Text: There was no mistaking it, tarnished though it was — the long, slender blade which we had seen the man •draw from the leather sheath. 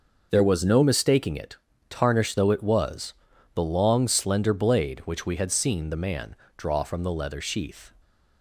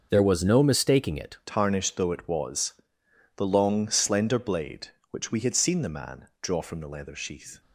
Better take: first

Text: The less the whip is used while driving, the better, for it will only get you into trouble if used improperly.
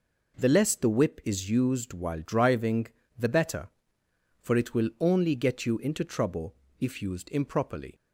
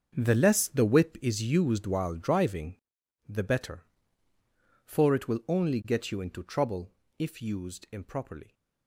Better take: first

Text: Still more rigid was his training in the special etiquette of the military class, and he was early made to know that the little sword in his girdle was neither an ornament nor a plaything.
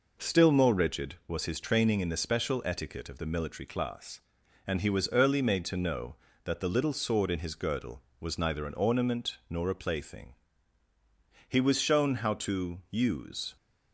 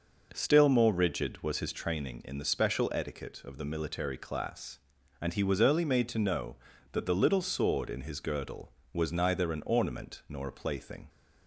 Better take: second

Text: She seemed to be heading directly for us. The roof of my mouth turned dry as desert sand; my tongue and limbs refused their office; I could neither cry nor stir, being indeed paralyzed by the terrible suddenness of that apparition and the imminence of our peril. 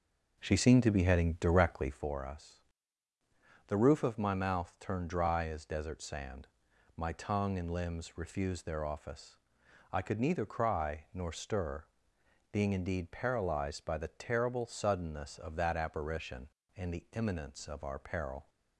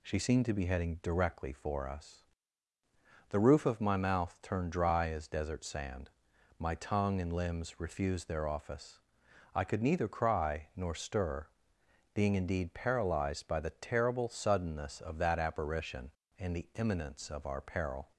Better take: second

